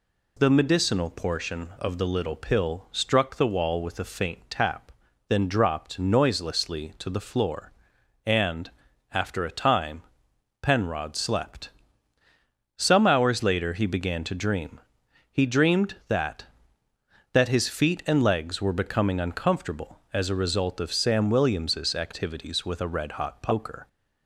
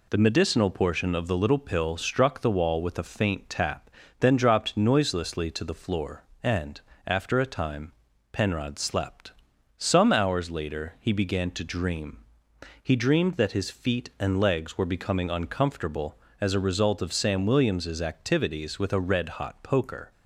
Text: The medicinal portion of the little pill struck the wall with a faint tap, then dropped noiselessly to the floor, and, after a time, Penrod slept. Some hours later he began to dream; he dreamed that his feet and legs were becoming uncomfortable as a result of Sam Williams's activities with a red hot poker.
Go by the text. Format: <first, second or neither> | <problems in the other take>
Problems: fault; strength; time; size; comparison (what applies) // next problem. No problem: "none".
second | says "that" twice; at 17.3 s